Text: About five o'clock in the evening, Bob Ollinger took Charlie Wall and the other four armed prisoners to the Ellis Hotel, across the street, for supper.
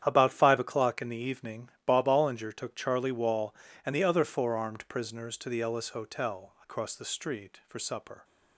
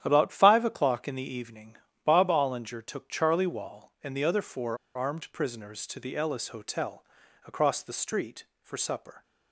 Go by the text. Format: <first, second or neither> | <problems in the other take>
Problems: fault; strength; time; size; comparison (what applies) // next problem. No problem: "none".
first | starts louder than the rest; strong; until 1.0 s; 10.5 dB; strong in the first // pauses between "four" and "armed"; slight; at 4.7 s; 0.19 s long